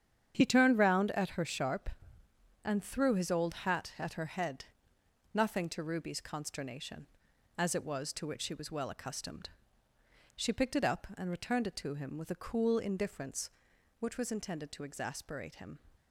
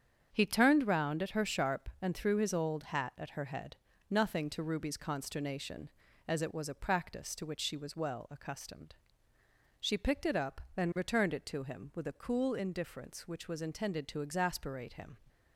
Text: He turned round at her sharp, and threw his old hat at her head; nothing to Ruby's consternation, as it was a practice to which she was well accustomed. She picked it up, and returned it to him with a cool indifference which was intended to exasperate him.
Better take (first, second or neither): second